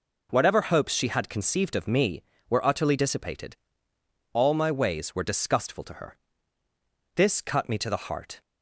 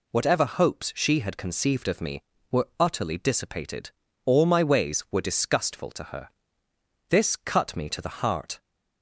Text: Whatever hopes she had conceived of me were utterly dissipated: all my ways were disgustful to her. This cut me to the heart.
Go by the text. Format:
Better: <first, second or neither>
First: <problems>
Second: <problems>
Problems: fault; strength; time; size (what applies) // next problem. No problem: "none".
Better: neither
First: none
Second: none